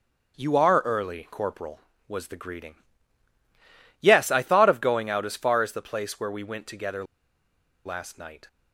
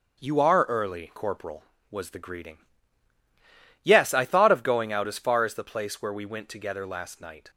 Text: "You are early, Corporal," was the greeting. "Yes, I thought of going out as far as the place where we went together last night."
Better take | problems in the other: second | starts louder than the rest; until 1.3 s; 6.5 dB; also in the second // pauses between "together" and "last"; noticeable; at 7.0 s; 0.81 s long

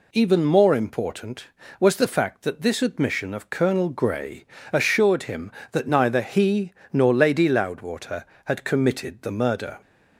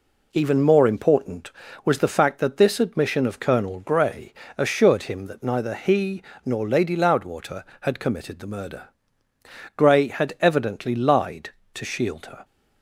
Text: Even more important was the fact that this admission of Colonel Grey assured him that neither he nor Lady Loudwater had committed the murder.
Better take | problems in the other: first | pauses between "Grey" and "assured"; slight; at 4.3 s; 0.24 s long; slight in the first // pauses between "he" and "nor"; slight; at 6.2 s; 0.22 s long; slight in the first // goes on to say "Grey had evidently lied to shield her"; strong; from 9.7 s on; 2.6 s long

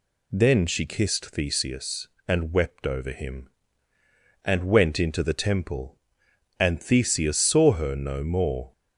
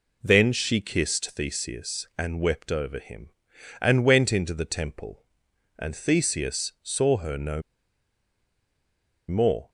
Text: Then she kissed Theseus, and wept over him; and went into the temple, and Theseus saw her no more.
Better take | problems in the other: first | pauses between "no" and "more"; strong; at 7.6 s; 1.6 s long

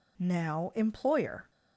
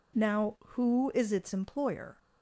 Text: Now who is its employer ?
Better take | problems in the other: second | skips "who is its"; at 0.7 s

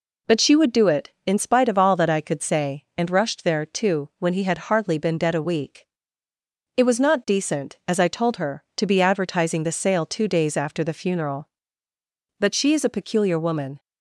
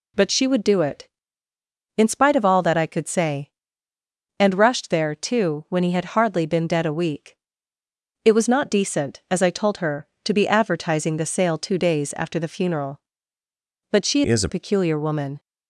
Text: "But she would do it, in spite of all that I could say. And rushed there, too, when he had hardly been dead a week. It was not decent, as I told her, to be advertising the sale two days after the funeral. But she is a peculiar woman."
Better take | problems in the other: first | changes voice from "is" to "a"; from 14.2 to 14.4 s; 0.2 s long

